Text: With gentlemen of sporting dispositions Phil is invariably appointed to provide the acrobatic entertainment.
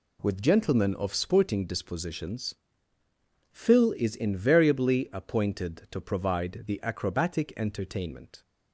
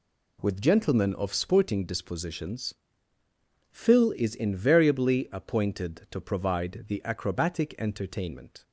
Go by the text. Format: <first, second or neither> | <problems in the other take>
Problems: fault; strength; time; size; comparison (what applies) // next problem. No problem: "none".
neither | pauses between "dispositions" and "Phil"; noticeable; the same in both